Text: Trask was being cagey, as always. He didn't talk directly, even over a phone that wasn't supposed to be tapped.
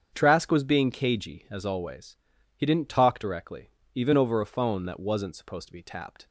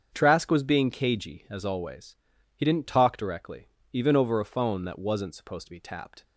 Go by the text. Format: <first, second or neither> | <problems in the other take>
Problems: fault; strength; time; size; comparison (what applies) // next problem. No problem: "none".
neither | starts louder than the rest; strong; the same in both